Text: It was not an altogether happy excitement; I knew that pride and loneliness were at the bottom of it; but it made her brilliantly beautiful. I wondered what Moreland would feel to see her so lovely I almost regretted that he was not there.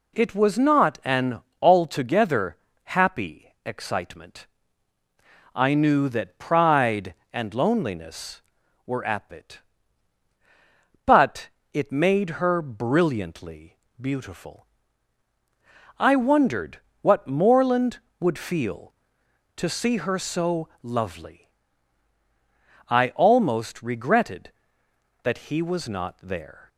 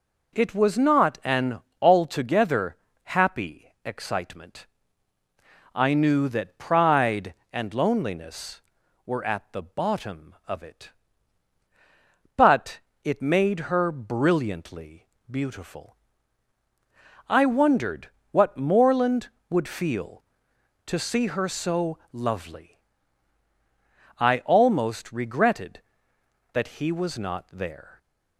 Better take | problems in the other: second | pauses between "an" and "altogether"; slight; at 1.4 s; 0.18 s long; slight in the second // pauses between "altogether" and "happy"; slight; at 2.5 s; 0.28 s long; slight in the second // skips "the bottom of"; at 9.3 s // pauses between "but" and "it"; slight; at 11.4 s; 0.24 s long; slight in the second // pauses between "brilliantly" and "beautiful"; slight; at 13.7 s; 0.24 s long; slight in the second // pauses between "wondered" and "what"; slight; at 16.7 s; 0.22 s long; slight in the second // pauses between "lovely" and "I"; strong; at 21.4 s; 1.4 s long; strong in the second

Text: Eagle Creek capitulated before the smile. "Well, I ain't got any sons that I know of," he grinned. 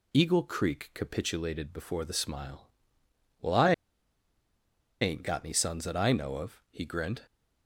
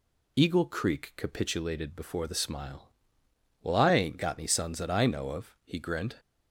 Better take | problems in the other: second | pauses between "I" and "ain't"; strong; at 3.7 s; 1.2 s long

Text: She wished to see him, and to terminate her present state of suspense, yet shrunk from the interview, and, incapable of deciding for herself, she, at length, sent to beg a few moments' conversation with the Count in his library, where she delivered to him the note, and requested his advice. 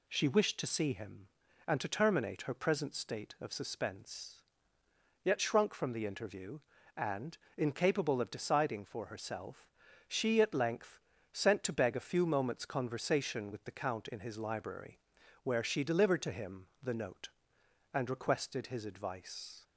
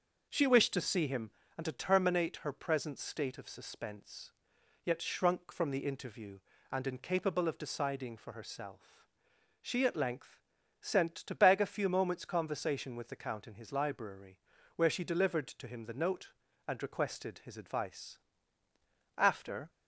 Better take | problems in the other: first | starts louder than the rest; until 1.5 s; 6 dB // goes on to say "After"; from 19.1 s on; 0.54 s long

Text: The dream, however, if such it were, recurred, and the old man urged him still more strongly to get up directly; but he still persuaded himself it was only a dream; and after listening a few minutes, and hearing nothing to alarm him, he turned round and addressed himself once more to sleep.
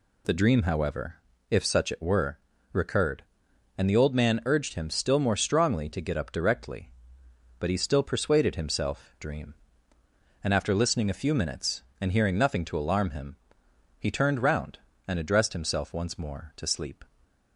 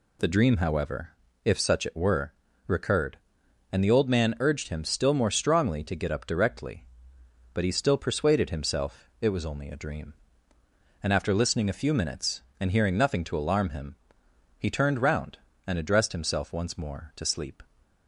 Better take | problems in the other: second | skips "it was only a"; at 9.1 s

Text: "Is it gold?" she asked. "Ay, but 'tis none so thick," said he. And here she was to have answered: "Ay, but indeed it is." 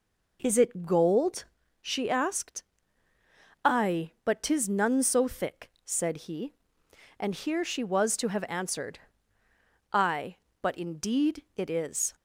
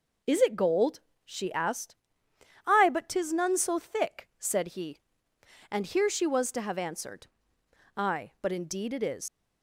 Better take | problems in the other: first | leaves "is" unfinished; at 9.2 s; 120 ms

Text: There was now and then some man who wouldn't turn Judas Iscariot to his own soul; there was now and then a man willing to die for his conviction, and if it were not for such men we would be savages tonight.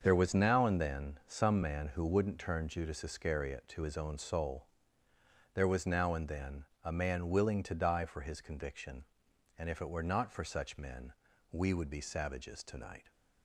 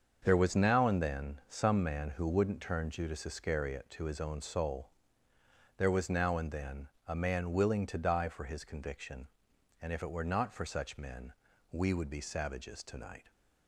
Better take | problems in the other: neither | starts louder than the rest; the same in both // pauses between "then" and "a"; slight; the same in both // pauses between "men" and "we"; the same in both

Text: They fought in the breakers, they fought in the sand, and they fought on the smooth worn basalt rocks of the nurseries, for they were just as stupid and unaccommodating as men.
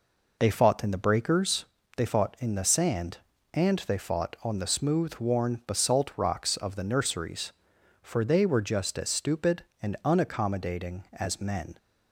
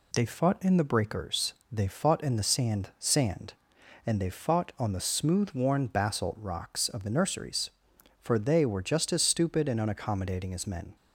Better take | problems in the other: first | says "sand" twice; at 2.9 s

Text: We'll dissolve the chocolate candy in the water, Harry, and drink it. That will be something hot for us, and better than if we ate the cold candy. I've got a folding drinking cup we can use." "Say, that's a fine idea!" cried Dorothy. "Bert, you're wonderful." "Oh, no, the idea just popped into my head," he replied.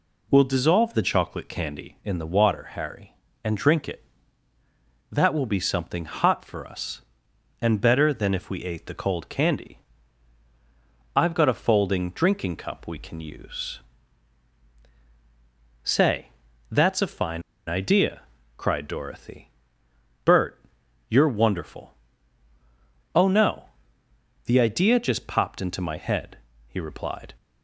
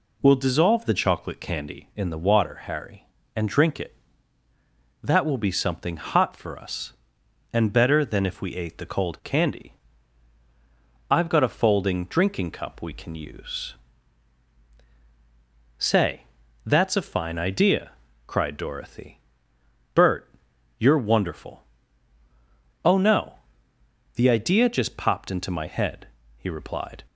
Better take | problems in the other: second | pauses between "fine" and "idea"; slight; at 17.4 s; 0.26 s long

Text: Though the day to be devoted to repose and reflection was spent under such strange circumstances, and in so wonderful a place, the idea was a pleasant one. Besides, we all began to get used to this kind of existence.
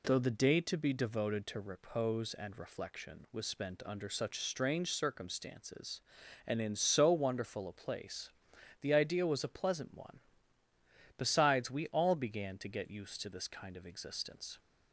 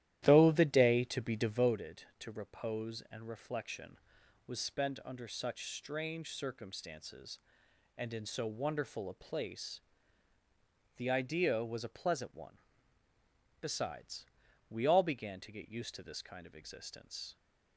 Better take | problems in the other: first | starts louder than the rest; strong; until 1.8 s; 13 dB

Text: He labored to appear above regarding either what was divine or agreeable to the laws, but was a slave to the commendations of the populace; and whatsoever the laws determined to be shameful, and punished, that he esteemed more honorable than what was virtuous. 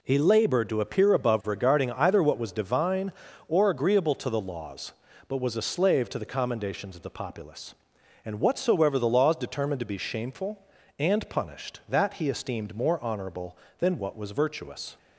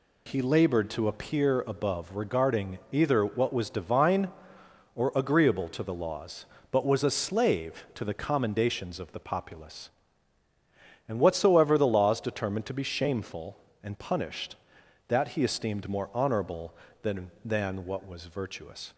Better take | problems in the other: first | says "than" twice; at 17.4 s

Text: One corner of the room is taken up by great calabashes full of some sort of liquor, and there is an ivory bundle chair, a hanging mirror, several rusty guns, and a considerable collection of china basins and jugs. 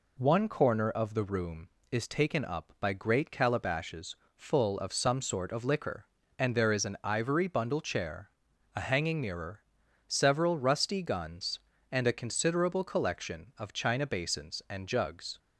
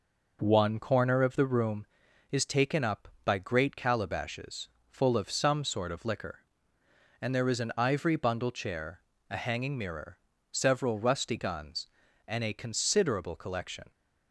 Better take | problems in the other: first | pauses between "calabashes" and "full"; slight; at 4.6 s; 0.20 s long; slight in the first // stops before "of china basins and jugs"; at 13.8 s

